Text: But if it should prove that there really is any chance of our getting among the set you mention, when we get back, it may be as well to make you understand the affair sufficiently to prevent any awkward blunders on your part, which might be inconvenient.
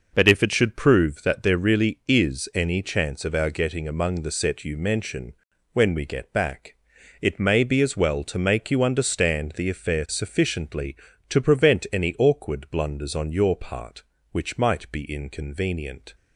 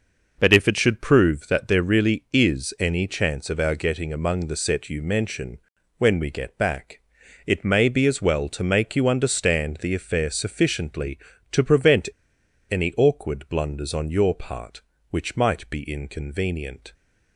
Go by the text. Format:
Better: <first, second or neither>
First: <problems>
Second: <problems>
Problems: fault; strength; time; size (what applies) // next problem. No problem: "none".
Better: first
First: none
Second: pauses between "prevent" and "any"; noticeable; at 12.0 s; 0.64 s long